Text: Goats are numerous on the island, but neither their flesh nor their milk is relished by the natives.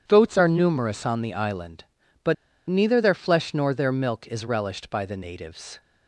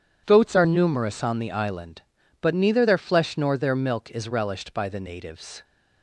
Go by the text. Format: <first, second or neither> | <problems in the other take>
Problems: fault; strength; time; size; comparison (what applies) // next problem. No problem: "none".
second | pauses between "but" and "neither"; slight; at 2.3 s; 0.35 s long